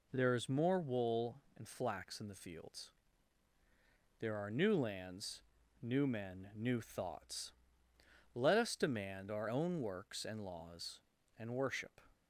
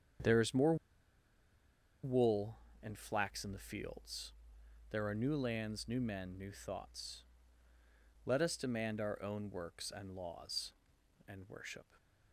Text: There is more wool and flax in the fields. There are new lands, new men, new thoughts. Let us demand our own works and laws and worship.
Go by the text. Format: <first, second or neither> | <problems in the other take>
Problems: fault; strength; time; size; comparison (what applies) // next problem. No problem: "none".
first | starts louder than the rest; strong; until 2.5 s; 8.5 dB // pauses between "more" and "wool"; strong; at 0.7 s; 1.2 s long // stays silent after the last word; slight; from 11.8 s on; 0.5 s long